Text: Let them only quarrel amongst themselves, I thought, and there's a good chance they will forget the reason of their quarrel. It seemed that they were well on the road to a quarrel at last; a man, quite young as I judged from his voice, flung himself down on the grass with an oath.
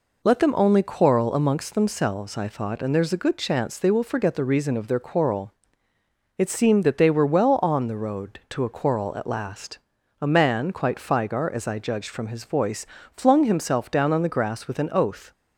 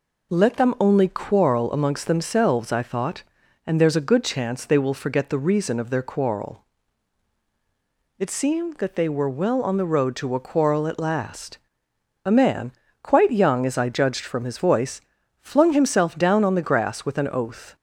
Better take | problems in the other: second | says "figar" for "young"; at 10.9 s

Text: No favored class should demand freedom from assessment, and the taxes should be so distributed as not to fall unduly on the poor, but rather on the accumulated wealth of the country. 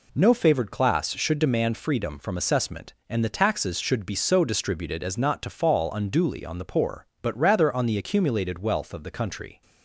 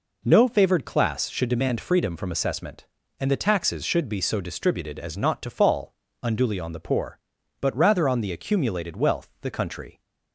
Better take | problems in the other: first | pauses between "fall" and "unduly"; slight; at 5.9 s; 0.30 s long // skips "of"; at 9.3 s

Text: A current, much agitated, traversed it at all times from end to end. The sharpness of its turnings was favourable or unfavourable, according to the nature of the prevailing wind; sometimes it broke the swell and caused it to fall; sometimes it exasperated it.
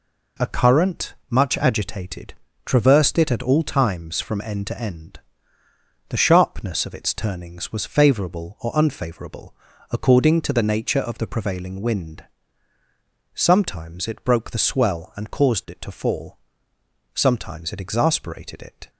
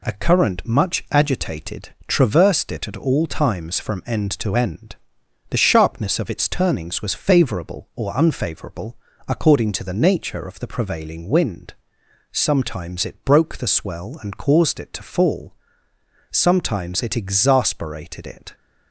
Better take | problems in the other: neither | none

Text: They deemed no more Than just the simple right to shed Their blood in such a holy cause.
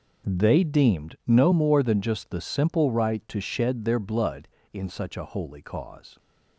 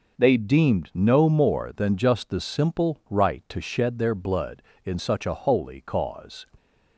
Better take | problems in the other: neither | none

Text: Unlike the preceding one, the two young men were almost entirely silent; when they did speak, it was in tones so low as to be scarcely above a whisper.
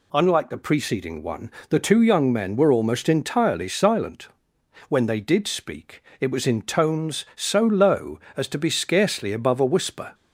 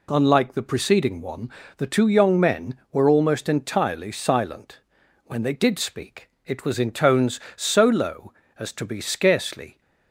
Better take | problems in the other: first | stops before "above a whisper"; at 9.8 s

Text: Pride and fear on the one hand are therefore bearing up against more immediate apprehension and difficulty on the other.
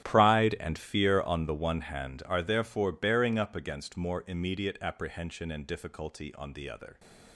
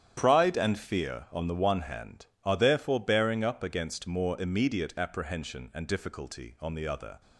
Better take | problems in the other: second | gets quieter; strong; throughout; 17 dB // starts louder than the rest; strong; until 1.1 s; 11 dB; strong in the second

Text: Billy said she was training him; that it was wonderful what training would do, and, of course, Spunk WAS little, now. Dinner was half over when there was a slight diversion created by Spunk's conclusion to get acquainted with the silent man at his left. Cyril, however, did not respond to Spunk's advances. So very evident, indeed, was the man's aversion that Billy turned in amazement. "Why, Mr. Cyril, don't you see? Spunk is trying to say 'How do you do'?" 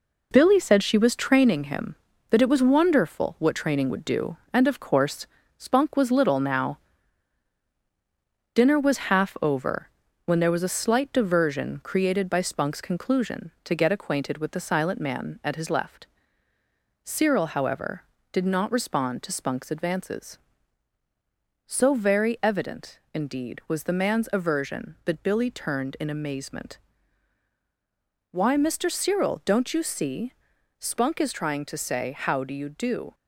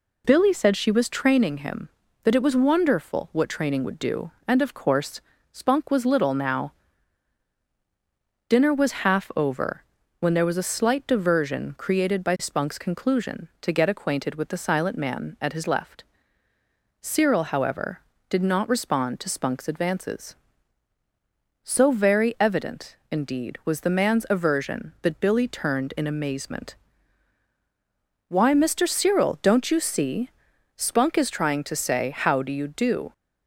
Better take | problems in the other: second | gets quieter; noticeable; throughout; 5 dB // pauses between "over" and "when"; slight; at 9.8 s; 0.36 s long; slight in the second

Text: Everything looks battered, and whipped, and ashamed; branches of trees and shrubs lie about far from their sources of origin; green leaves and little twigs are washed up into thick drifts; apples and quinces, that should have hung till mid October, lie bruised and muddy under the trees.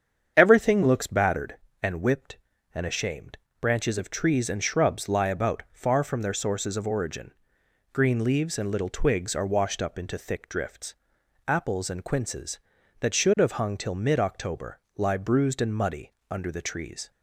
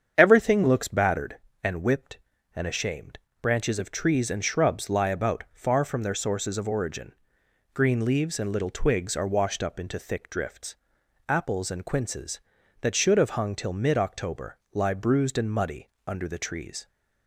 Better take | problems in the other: neither | starts louder than the rest; strong; the same in both // pauses between "muddy" and "under"; slight; the same in both

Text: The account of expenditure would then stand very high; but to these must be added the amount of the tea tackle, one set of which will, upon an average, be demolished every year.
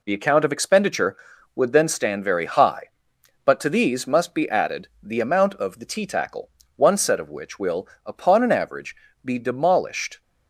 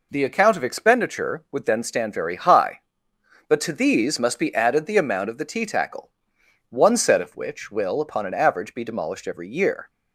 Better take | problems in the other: second | stops before "every year"; at 10.2 s

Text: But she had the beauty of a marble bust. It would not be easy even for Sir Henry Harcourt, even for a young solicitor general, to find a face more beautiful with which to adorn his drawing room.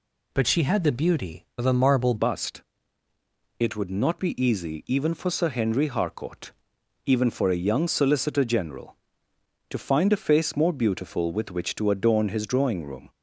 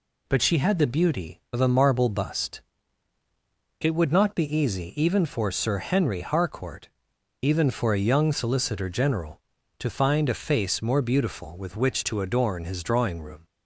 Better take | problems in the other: second | changes voice at "bust"; from 2.1 s on; 10.9 s long

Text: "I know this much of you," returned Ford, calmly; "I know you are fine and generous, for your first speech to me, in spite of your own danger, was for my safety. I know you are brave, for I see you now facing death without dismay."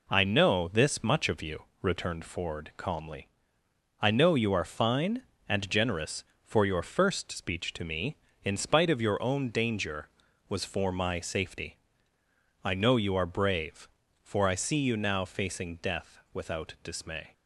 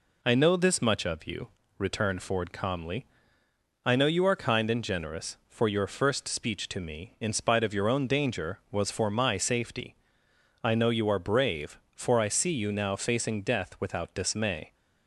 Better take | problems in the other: first | says "kind" for "fine"; at 4.3 s

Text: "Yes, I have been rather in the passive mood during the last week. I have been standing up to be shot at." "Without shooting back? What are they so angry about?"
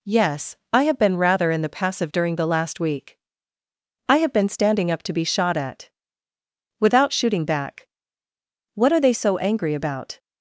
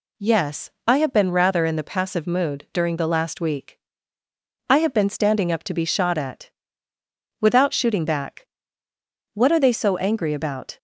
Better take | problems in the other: second | skips "mood"; at 2.1 s

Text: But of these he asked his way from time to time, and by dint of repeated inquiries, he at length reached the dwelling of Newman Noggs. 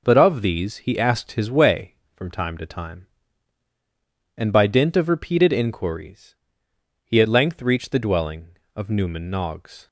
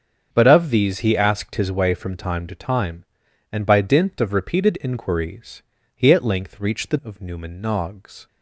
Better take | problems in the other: first | starts louder than the rest; strong; until 1.3 s; 7.5 dB // skips "dwelling"; at 7.0 s

